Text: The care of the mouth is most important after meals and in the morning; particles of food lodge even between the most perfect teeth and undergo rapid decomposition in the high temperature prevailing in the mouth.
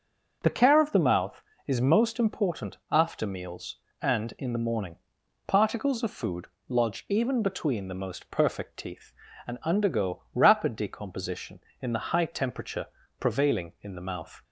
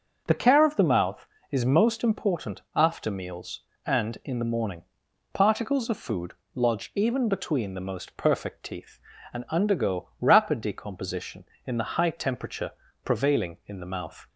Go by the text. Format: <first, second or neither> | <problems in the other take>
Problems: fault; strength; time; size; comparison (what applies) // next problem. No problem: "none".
neither | starts louder than the rest; the same in both // pauses between "food" and "lodge"; slight; the same in both // pauses between "temperature" and "prevailing"; slight; the same in both